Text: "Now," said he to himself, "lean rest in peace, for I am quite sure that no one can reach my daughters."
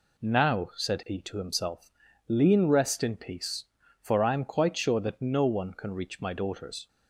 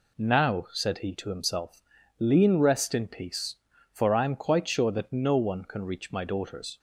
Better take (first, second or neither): neither